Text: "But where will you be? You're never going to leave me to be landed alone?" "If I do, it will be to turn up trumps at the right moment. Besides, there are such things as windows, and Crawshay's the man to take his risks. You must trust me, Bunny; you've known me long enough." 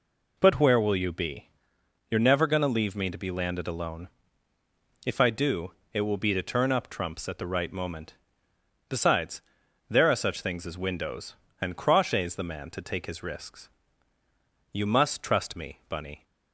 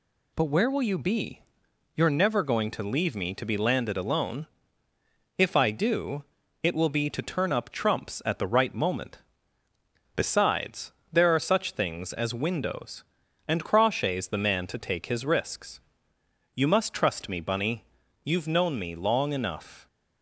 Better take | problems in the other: second | stops before "you've known me long enough"; at 16.2 s

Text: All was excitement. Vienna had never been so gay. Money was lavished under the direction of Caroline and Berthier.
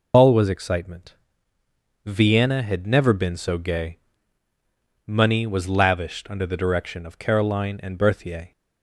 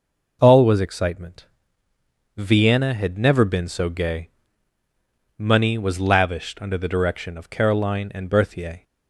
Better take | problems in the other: second | loses the start of "All"; at 0.1 s; 50 ms

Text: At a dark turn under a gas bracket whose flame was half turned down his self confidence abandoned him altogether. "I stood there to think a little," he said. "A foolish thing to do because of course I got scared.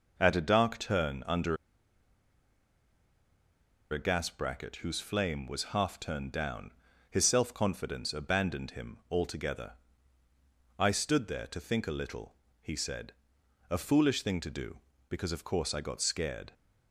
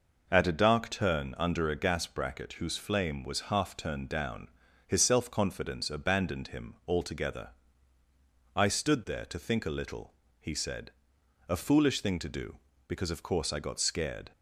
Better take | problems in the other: second | pauses between "under" and "a"; strong; at 1.5 s; 2.3 s long // pauses between "down" and "his"; slight; at 6.7 s; 0.36 s long; slight in the second

